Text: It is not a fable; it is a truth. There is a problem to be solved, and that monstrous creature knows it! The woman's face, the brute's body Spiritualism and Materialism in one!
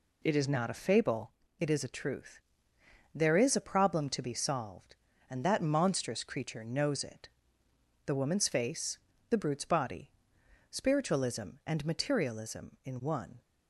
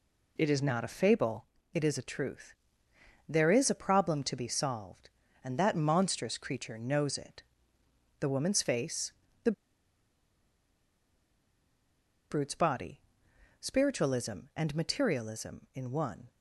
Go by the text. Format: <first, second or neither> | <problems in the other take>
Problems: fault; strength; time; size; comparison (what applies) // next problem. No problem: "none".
first | pauses between "the" and "brute's"; strong; at 9.5 s; 2.7 s long // pauses between "body" and "Spiritualism"; noticeable; at 13.0 s; 0.58 s long; noticeable in the first